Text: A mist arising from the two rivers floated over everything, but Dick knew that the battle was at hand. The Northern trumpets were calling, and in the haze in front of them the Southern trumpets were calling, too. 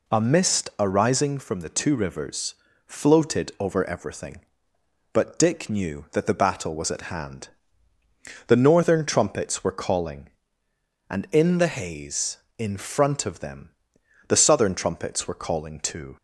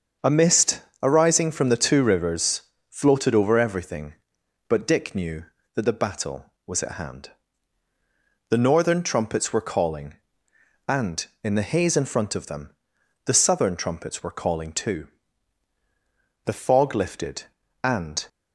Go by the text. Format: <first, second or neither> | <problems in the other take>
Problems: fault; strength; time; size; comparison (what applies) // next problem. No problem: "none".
first | starts louder than the rest; until 1.4 s; 6.5 dB // pauses between "mist" and "arising"; slight; at 0.8 s; 0.20 s long // pauses between "rivers" and "floated"; slight; at 2.6 s; 0.28 s long; slight in the first // pauses between "them" and "the"; noticeable; at 12.7 s; 0.56 s long; noticeable in the first // goes on to say "The fog lifted and"; strong; from 16.4 s on; 1.8 s long